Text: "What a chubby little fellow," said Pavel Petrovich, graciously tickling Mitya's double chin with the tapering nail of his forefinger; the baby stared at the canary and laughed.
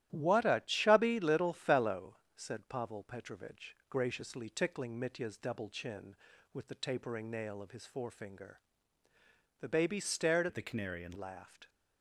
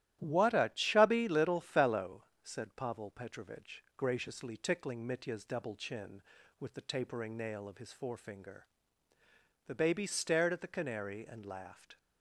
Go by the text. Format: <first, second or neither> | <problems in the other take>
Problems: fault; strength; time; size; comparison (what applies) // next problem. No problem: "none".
second | starts louder than the rest; strong; until 1.1 s; 12.5 dB; strong in the second // changes voice from "at" to "and"; from 10.4 to 11.1 s; 0.7 s long